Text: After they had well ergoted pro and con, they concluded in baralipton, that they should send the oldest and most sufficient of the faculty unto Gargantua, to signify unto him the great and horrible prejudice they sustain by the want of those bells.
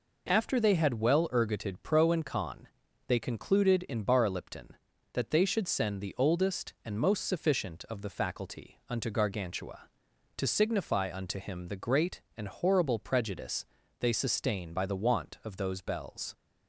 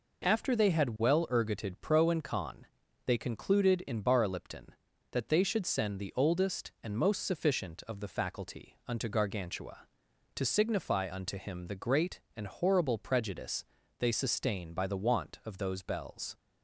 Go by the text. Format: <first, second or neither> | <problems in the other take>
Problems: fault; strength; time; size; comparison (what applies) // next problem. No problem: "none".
neither | pauses between "prejudice" and "they"; slight; the same in both